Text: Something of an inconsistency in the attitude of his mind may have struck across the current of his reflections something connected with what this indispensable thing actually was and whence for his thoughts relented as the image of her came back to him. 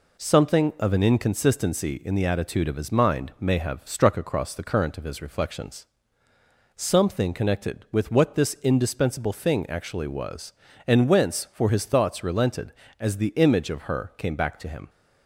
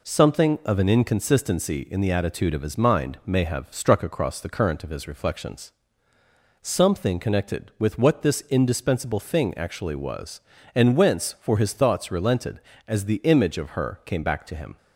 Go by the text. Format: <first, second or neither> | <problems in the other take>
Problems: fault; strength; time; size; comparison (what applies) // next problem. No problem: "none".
neither | pauses between "reflections" and "something"; noticeable; the same in both